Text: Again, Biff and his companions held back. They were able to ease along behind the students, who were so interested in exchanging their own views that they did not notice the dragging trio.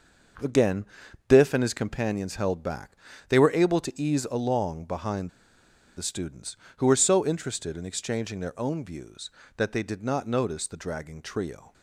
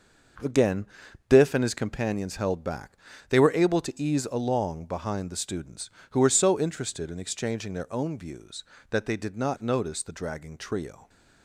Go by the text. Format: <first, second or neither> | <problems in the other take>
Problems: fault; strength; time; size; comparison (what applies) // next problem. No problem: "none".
second | pauses between "behind" and "the"; noticeable; at 5.2 s; 0.67 s long